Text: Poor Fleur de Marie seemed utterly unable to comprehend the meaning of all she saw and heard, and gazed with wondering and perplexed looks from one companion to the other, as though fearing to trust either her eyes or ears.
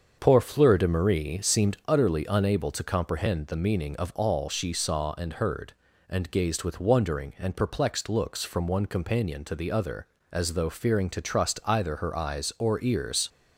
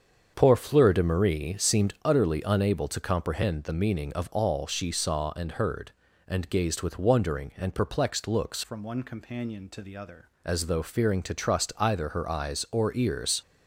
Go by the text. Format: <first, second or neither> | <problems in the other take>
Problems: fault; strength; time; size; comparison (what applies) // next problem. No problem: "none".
first | starts louder than the rest; strong; until 1.3 s; 7 dB; also in the first // changes voice from "from" to "other"; from 8.6 to 10.2 s; 1.6 s long